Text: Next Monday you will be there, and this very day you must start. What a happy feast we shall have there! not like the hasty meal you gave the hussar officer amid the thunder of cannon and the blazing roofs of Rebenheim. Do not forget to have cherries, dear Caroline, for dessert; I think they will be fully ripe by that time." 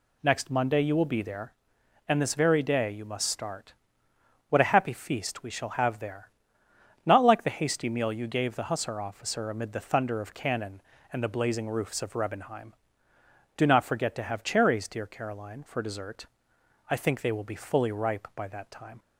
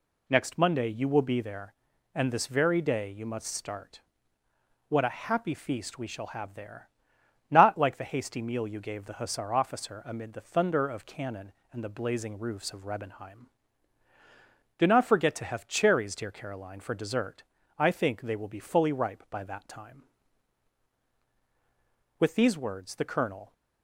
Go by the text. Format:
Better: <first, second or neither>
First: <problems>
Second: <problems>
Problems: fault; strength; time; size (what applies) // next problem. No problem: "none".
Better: first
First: none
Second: goes on to say "With these words the colonel"; from 22.1 s on; 1.3 s long